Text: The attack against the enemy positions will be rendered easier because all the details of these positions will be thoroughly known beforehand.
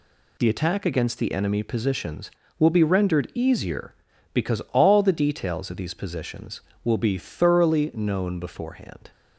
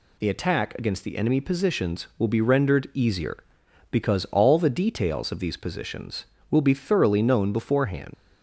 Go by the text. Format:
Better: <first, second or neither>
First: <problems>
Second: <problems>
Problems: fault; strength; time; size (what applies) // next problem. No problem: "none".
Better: first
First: none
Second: leaves "beforehand" unfinished; at 8.1 s; 80 ms